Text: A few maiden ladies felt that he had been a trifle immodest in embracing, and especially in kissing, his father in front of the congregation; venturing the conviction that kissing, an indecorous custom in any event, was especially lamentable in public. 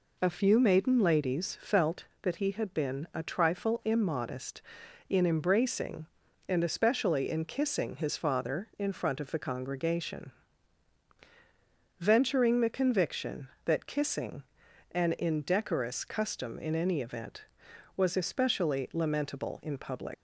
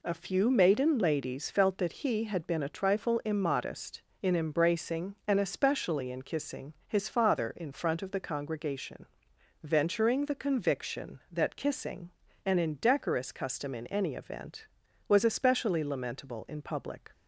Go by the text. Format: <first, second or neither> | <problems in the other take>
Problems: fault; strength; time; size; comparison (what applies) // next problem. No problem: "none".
second | leaves "public" unfinished; at 20.1 s; 165 ms